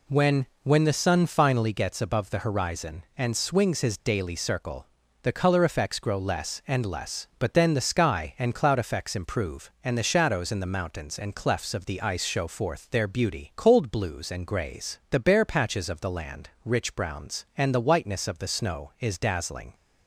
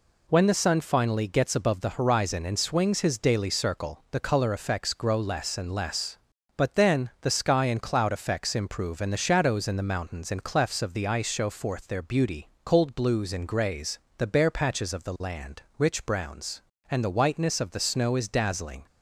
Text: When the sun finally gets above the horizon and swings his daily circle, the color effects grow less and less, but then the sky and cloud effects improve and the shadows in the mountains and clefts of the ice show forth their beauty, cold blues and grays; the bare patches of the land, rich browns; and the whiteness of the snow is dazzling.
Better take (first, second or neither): second